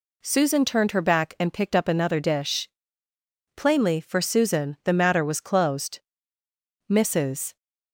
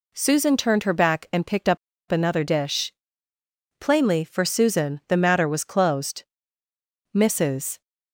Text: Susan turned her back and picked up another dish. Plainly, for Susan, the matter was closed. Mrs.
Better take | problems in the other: first | pauses between "up" and "another"; slight; at 1.7 s; 0.33 s long

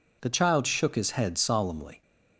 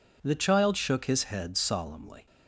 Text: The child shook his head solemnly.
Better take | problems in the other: neither | none

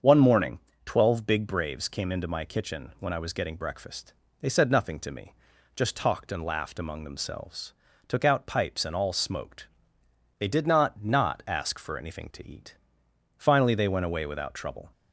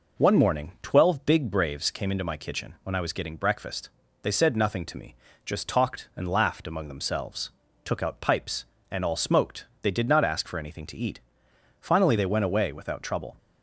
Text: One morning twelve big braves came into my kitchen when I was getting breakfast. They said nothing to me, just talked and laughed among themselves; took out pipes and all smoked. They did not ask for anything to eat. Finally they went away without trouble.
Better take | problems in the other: second | starts louder than the rest; until 1.2 s; 7 dB // pauses between "morning" and "twelve"; slight; at 0.6 s; 0.26 s long // says "not" twice; at 11.0 s

